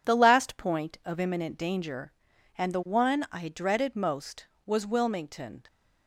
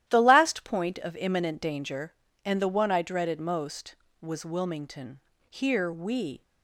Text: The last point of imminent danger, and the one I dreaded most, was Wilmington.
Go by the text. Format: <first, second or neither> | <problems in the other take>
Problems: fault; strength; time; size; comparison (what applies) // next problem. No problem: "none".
first | starts louder than the rest; strong; until 1.0 s; 12.5 dB // goes on to say "Here we"; noticeable; from 5.4 s on; 0.93 s long